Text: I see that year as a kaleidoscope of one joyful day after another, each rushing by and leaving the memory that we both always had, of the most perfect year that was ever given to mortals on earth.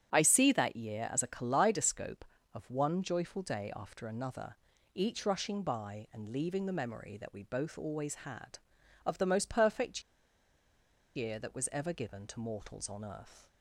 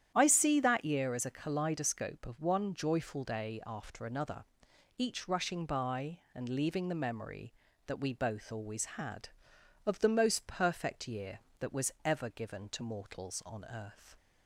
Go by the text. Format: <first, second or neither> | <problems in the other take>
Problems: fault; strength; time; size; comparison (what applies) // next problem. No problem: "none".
second | starts louder than the rest; strong; until 1.1 s; 9.5 dB; strong in the second // pauses between "perfect" and "year"; at 10.0 s; 1.1 s long